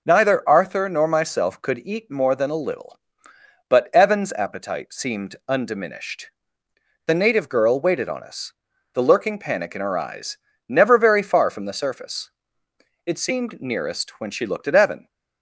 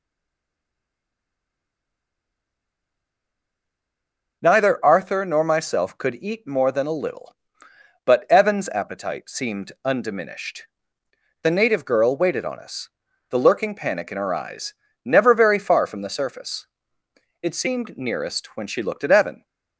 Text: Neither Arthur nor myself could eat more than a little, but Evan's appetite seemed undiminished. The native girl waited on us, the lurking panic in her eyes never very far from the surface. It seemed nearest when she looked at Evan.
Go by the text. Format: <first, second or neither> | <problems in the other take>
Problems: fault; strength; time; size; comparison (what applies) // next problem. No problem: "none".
first | stays silent before the first word; strong; until 4.4 s; 4.4 s long // pauses between "eyes" and "never"; slight; at 14.7 s; 0.30 s long; slight in the first